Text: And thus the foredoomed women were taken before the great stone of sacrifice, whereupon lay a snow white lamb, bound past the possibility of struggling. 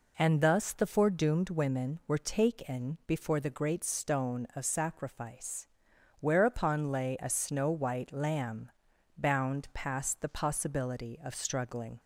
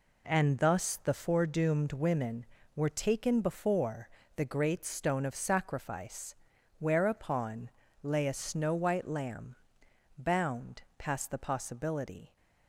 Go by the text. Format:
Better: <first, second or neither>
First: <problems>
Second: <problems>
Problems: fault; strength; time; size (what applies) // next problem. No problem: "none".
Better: first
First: none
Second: pauses between "before" and "the"; slight; at 4.0 s; 0.28 s long // pauses between "whereupon" and "lay"; slight; at 7.6 s; 0.32 s long // pauses between "bound" and "past"; slight; at 10.8 s; 0.16 s long // stops before "of struggling"; at 12.3 s